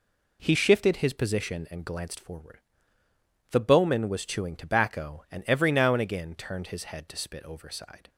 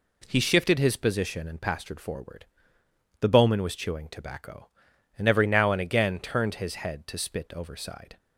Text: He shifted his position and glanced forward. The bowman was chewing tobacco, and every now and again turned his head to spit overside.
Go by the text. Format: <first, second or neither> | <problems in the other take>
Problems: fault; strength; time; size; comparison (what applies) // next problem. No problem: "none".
first | says "pastured" for "glanced"; at 1.6 s